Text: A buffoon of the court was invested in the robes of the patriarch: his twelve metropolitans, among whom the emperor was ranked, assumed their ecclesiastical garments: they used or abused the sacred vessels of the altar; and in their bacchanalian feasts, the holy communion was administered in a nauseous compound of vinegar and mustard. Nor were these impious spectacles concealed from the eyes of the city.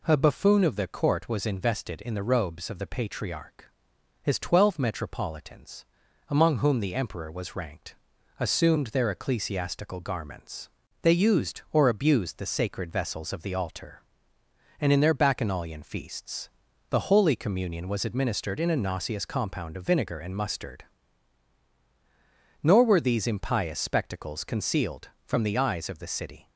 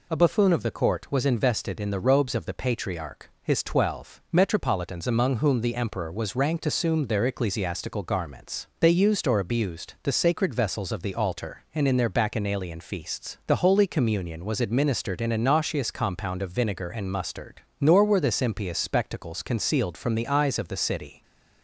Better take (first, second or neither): first